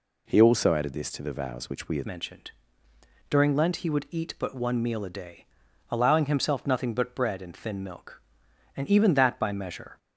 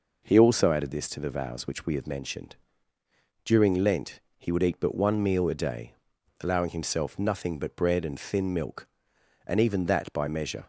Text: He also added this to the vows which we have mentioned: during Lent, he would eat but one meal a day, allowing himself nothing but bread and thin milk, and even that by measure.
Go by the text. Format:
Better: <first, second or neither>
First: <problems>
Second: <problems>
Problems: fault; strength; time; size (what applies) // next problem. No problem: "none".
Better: second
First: changes voice at "mentioned"; from 2.0 s on; 7.9 s long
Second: none